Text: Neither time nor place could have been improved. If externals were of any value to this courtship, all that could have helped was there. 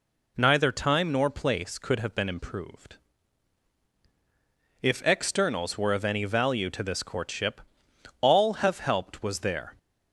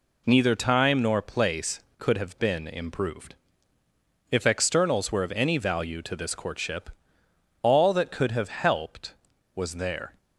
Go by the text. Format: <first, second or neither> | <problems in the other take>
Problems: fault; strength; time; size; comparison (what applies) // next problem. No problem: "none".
second | skips "that could"; at 8.5 s